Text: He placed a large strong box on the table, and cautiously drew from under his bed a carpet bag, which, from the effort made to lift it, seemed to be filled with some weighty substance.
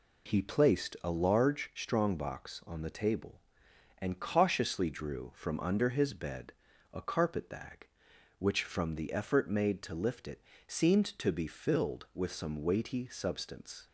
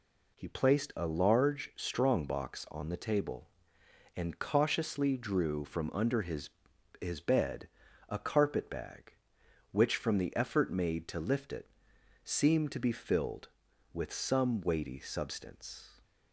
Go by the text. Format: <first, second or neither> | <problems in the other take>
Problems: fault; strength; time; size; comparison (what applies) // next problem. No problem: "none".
first | says "his" twice; at 7.0 s // pauses between "bed" and "a"; at 7.6 s; 0.40 s long; also in the first